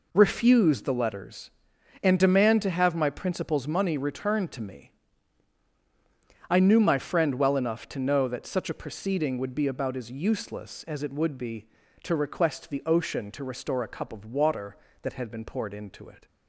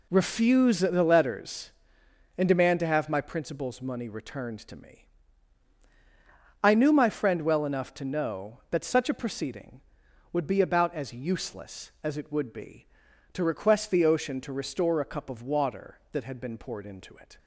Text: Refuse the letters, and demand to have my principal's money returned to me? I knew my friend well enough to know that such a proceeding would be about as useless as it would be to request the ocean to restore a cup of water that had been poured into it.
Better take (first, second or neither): neither